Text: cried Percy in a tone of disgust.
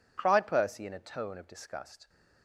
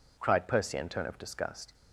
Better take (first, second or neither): first